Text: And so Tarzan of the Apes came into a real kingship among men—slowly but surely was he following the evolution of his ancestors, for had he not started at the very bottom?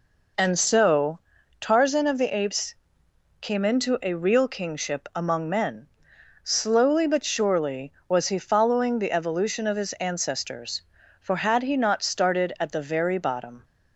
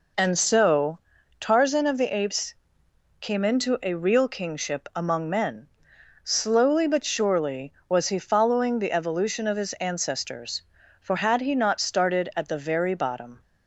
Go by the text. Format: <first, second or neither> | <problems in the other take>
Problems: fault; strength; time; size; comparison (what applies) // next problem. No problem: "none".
neither | pauses between "so" and "Tarzan"; the same in both // pauses between "Apes" and "came"; noticeable; the same in both